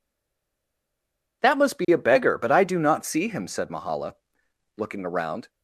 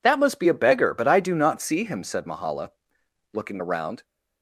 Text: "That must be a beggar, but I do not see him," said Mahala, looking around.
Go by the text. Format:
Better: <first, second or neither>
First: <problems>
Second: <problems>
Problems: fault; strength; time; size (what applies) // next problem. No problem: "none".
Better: second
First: stays silent before the first word; noticeable; until 1.4 s; 1.4 s long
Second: none